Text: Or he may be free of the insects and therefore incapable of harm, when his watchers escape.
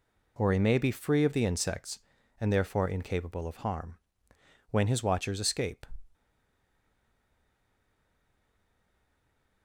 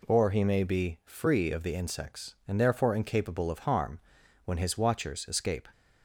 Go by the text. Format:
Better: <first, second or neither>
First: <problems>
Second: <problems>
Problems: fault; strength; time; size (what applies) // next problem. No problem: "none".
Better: second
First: stays silent after the last word; strong; from 6.1 s on; 3.5 s long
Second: none